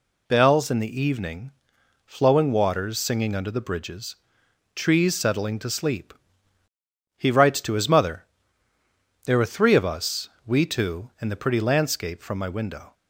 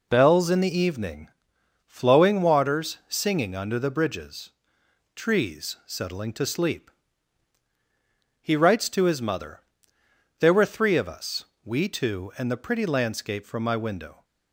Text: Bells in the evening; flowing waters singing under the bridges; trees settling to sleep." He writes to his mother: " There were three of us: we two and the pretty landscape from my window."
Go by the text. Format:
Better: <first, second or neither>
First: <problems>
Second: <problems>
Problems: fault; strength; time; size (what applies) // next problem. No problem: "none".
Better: neither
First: none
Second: none